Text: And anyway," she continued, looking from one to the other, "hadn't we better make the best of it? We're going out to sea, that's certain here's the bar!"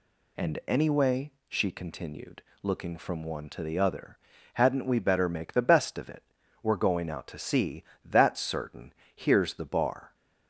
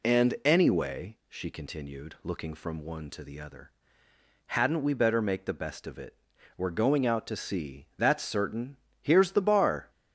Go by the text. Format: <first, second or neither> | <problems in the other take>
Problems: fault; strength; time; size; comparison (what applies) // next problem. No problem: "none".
neither | pauses between "certain" and "here's"; slight; the same in both